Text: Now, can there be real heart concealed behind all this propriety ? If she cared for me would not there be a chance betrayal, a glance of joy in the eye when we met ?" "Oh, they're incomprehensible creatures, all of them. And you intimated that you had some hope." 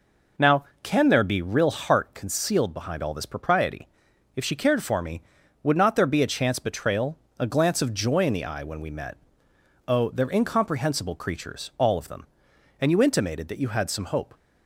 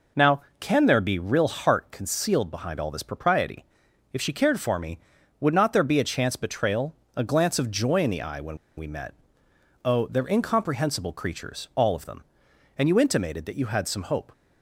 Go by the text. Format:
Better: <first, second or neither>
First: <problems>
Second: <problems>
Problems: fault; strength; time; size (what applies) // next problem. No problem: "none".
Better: first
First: none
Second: pauses between "when" and "we"; slight; at 8.5 s; 0.19 s long